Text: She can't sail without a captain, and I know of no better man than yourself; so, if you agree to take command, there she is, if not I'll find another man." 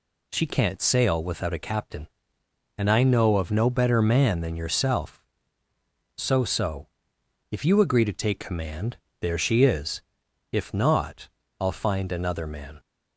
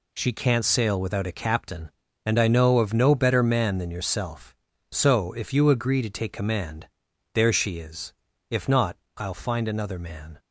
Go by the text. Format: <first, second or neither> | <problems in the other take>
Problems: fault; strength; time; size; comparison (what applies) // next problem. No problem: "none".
second | says "so" twice; at 6.4 s // pauses between "not" and "I'll"; slight; at 11.2 s; 0.30 s long; slight in the second